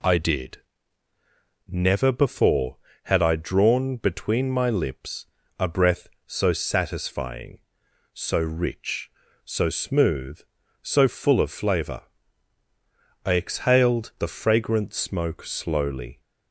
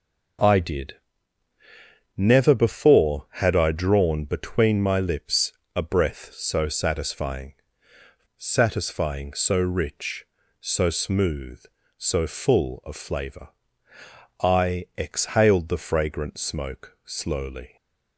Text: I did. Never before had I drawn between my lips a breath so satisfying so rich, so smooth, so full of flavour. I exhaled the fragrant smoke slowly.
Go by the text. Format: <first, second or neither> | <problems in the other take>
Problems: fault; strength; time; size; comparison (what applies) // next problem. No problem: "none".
first | pauses between "lips" and "a"; slight; at 5.5 s; 0.24 s long; slight in the first // says "satisfying" twice; at 8.4 s